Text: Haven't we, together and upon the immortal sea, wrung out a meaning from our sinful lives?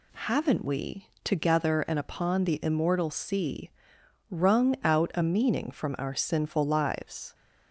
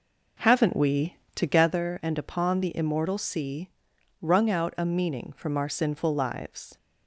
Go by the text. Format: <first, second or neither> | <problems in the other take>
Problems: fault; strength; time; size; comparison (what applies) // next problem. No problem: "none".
first | starts louder than the rest; noticeable; until 1.8 s; 4.5 dB